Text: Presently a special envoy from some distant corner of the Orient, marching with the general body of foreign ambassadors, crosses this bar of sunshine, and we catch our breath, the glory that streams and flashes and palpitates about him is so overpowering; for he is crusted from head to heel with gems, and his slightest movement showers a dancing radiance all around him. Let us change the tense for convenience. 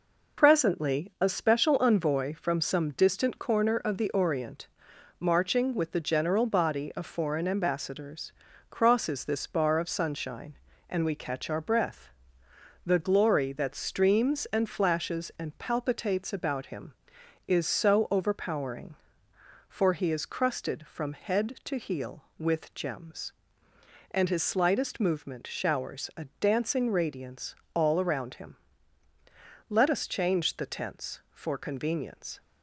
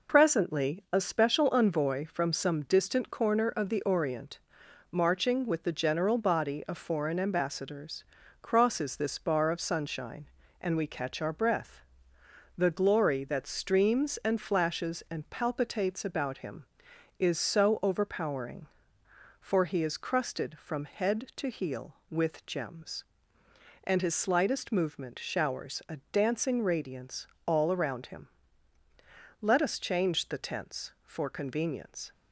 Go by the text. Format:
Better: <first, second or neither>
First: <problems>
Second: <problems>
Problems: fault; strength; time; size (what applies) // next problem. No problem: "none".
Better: neither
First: pauses between "radiance" and "all"; slight; at 27.5 s; 0.18 s long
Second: pauses between "radiance" and "all"; slight; at 27.2 s; 0.18 s long